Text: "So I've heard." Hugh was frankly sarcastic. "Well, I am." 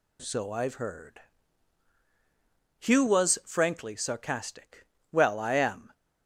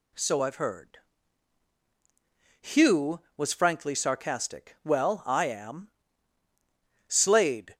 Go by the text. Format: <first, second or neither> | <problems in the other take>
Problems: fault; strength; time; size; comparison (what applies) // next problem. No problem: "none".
first | goes on to say "Slade"; noticeable; from 7.0 s on; 0.68 s long